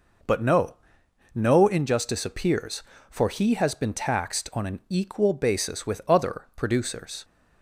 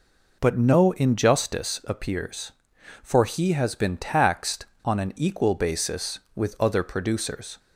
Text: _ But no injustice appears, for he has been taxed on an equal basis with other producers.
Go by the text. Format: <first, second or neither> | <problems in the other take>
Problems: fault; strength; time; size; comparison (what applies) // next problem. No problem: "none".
second | says "no" twice; at 1.3 s